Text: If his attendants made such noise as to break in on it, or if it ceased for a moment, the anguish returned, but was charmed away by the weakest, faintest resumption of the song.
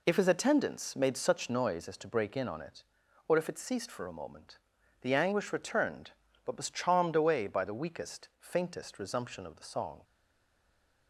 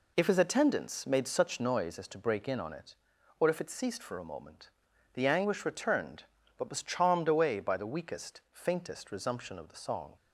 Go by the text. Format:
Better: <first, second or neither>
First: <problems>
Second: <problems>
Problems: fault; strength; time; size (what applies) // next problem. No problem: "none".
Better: second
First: stays silent after the last word; from 10.0 s on; 1.0 s long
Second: none